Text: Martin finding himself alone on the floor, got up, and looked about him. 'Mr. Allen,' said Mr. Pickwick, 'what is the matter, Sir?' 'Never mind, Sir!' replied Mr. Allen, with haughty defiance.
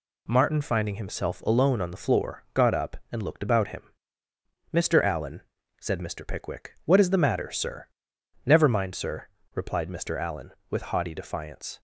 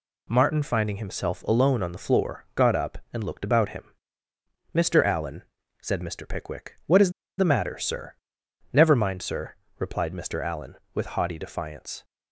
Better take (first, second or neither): first